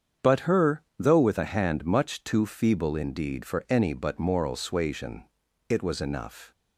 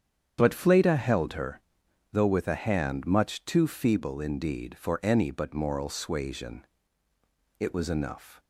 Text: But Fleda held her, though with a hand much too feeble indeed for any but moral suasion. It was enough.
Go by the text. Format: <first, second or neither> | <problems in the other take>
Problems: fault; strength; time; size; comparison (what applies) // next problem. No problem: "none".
second | starts louder than the rest; strong; until 1.3 s; 7.5 dB; strong in the second // skips "Fleda held"; at 0.4 s